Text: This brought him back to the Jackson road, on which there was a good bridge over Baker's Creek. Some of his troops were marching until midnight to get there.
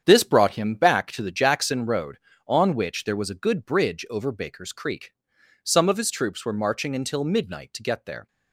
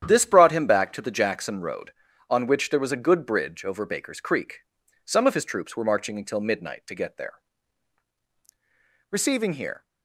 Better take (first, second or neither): first